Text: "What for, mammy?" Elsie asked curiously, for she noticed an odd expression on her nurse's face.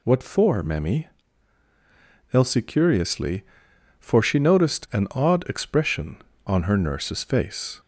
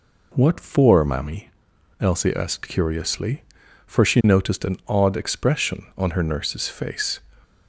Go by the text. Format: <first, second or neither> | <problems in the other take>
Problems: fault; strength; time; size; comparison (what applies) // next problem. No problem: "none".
second | skips "asked"; at 2.6 s